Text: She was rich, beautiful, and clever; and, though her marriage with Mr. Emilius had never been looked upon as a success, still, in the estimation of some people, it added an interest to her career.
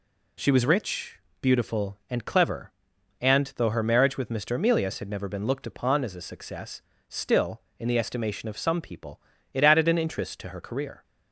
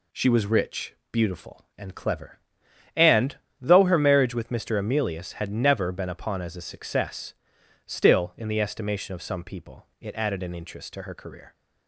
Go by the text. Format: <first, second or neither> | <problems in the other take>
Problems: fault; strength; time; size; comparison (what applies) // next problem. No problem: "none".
first | skips "looked"; at 6.0 s